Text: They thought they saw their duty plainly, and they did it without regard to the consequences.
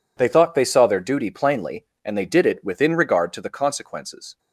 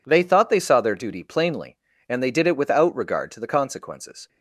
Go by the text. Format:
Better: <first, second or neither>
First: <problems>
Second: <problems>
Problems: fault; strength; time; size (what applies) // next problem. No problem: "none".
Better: second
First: says "within" for "without"; at 2.6 s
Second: none